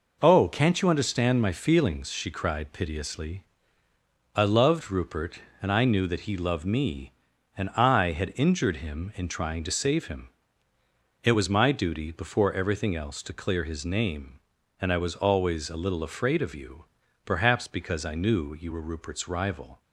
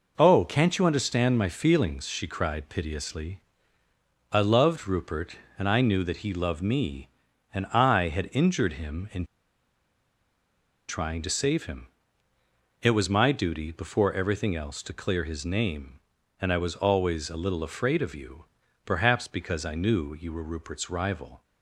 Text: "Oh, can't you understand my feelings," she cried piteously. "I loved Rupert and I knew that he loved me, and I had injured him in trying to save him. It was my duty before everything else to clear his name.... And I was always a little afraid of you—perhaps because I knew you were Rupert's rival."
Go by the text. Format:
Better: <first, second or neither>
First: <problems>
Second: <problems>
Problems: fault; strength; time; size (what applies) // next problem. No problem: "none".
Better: first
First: none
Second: pauses between "in" and "trying"; strong; at 9.2 s; 1.6 s long